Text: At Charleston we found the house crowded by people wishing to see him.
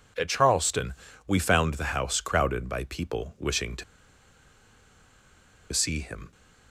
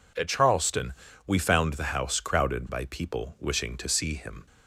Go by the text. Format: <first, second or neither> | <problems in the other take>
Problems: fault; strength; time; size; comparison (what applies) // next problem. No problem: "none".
second | pauses between "Charleston" and "we"; slight; at 0.9 s; 0.34 s long; slight in the second // pauses between "to" and "see"; strong; at 3.8 s; 1.8 s long